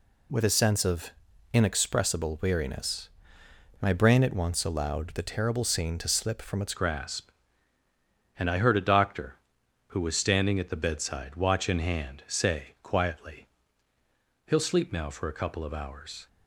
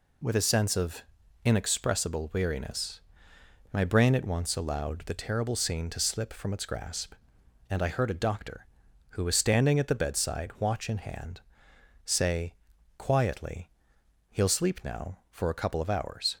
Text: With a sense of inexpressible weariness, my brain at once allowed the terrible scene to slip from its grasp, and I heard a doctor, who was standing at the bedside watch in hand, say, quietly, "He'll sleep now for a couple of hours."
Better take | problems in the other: second | pauses between "of" and "inexpressible"; at 1.1 s; 0.42 s long; also in the second // changes voice at "grasp"; from 6.7 s on; 9.5 s long

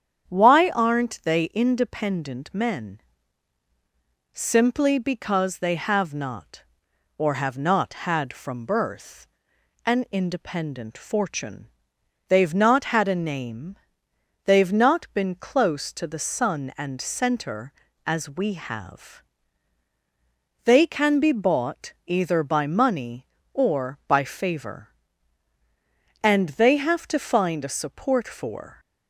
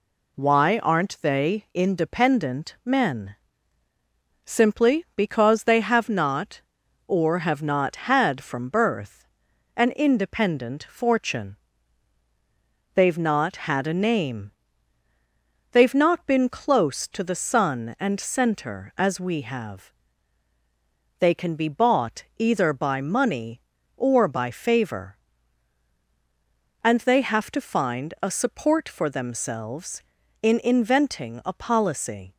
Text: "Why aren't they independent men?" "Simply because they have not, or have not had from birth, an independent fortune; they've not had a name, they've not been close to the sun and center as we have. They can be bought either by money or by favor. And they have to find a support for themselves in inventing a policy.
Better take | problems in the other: second | starts louder than the rest; strong; until 1.3 s; 8.5 dB // stops before "themselves in inventing a policy"; at 28.7 s

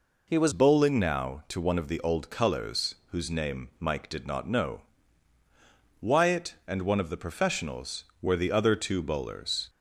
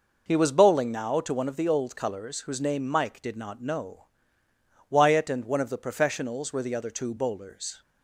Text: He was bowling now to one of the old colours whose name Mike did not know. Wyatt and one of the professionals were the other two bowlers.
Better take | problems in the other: second | changes voice at "bowling"; from 0.5 s on; 9.1 s long // pauses between "colours" and "whose"; slight; at 2.9 s; 0.16 s long

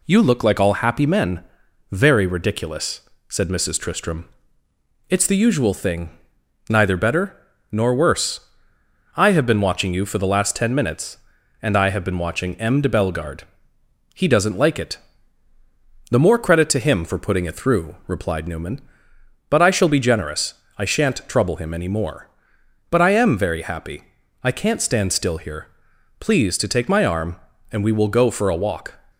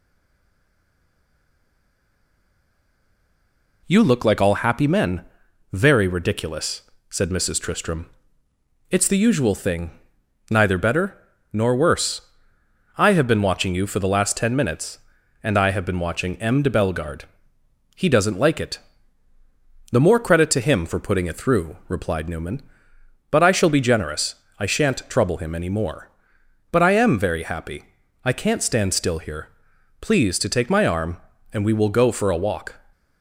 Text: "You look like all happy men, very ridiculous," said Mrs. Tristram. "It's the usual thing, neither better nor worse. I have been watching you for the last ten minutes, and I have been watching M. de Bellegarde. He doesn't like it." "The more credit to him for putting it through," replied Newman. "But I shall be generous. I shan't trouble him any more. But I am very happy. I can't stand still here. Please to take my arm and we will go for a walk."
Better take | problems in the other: first | stays silent before the first word; strong; until 3.8 s; 3.8 s long // pauses between "better" and "nor"; at 11.1 s; 0.38 s long; also in the first

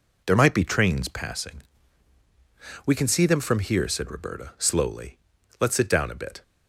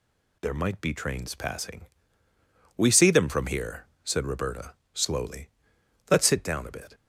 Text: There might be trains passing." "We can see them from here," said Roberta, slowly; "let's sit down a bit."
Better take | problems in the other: first | skips "can"; at 2.9 s

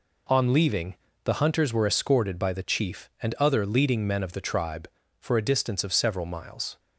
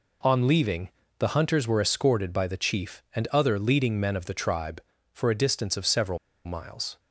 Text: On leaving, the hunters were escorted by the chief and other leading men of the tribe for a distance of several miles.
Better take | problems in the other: first | pauses between "several" and "miles"; slight; at 6.1 s; 0.28 s long

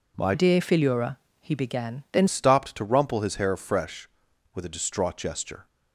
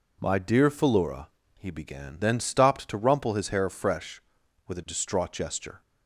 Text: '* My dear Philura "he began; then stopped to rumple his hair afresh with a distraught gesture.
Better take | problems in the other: second | changes voice from "dear" to "then"; from 0.3 to 2.2 s; 1.9 s long // pauses between "Philura" and "he"; slight; at 1.1 s; 0.24 s long; slight in the second

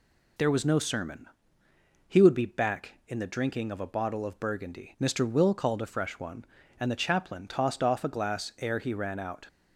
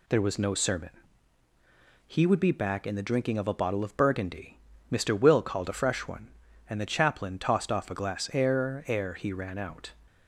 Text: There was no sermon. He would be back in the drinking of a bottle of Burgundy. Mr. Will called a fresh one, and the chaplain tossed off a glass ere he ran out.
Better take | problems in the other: first | says "ere" twice; at 8.8 s

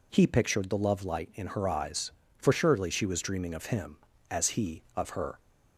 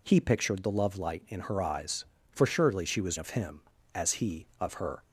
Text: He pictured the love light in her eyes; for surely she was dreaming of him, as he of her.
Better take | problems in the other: first | skips "dreaming"; at 3.1 s

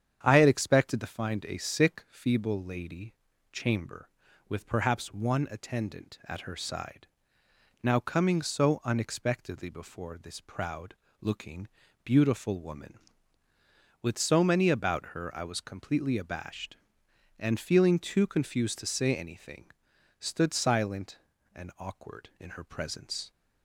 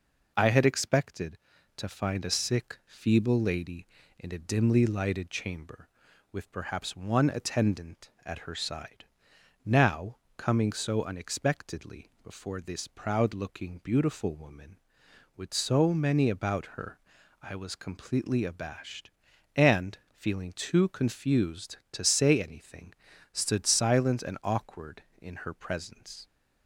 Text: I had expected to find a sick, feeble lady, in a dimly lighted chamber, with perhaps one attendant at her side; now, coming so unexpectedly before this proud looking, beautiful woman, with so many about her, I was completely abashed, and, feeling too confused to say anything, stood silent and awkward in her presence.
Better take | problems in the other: second | starts louder than the rest; strong; until 1.2 s; 8.5 dB // skips "in a dimly lighted"; at 3.3 s // pauses between "proud" and "looking"; slight; at 10.9 s; 0.28 s long

